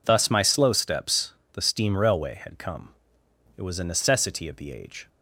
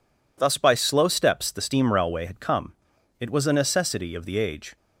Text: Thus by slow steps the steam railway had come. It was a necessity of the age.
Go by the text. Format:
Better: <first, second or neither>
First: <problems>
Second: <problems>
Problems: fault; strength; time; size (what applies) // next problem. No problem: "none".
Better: second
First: says "my" for "by"; at 0.2 s // pauses between "steps" and "the"; slight; at 1.3 s; 0.20 s long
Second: none